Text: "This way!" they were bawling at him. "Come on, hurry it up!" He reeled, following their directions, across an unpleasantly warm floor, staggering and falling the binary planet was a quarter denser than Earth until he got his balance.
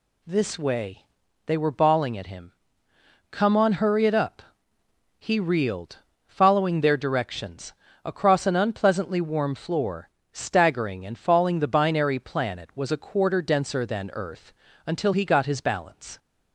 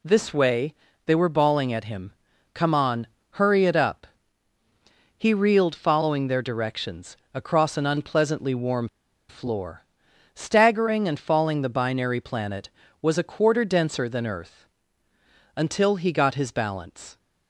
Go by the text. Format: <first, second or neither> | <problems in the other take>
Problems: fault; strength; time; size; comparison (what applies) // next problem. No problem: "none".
first | pauses between "warm" and "floor"; at 8.8 s; 0.42 s long // pauses between "Earth" and "until"; noticeable; at 14.6 s; 0.88 s long; slight in the first